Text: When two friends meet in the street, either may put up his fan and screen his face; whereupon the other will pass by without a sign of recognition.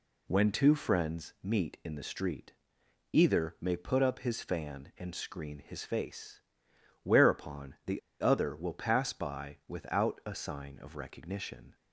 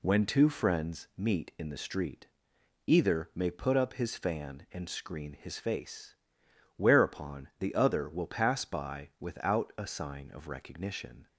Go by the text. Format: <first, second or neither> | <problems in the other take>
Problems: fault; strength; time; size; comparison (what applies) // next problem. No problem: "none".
second | pauses between "the" and "other"; slight; at 8.0 s; 0.20 s long